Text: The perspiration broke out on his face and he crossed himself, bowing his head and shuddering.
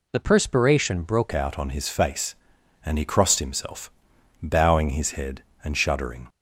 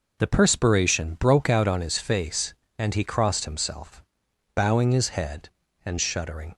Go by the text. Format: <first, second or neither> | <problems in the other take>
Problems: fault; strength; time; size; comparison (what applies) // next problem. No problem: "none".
second | changes voice at "out"; from 1.3 s on; 4.9 s long